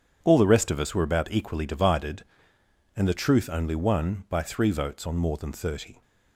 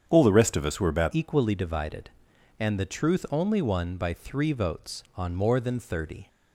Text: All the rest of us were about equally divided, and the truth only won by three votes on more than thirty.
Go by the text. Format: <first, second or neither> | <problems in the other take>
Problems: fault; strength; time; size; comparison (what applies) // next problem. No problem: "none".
first | starts louder than the rest; strong; until 1.0 s; 8 dB; strong in the first // changes voice at "equally"; from 1.1 s on; 5.1 s long